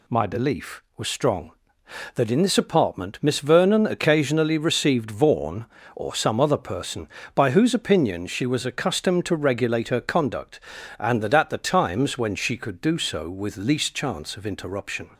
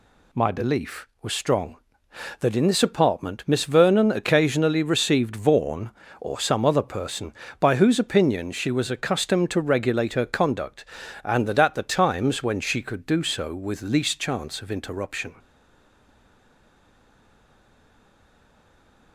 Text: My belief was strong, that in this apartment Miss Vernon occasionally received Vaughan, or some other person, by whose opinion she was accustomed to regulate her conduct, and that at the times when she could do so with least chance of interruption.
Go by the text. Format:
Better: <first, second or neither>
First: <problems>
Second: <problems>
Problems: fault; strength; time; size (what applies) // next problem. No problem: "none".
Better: first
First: none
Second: stays silent after the last word; strong; from 15.3 s on; 3.8 s long